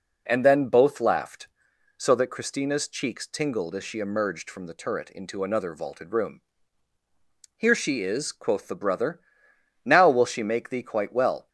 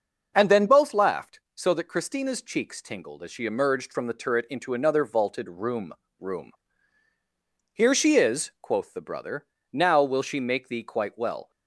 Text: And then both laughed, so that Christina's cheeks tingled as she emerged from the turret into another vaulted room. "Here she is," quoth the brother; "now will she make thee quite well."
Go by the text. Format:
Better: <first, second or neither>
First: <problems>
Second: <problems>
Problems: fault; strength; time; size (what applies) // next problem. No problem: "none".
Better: first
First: none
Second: starts louder than the rest; until 1.3 s; 6 dB // says "room" twice; at 6.1 s